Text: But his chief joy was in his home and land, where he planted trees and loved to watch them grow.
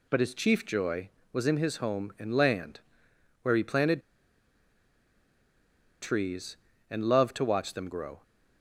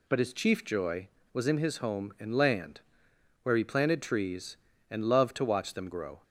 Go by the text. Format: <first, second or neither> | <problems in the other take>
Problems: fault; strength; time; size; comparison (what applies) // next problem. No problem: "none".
second | pauses between "planted" and "trees"; strong; at 4.0 s; 2.0 s long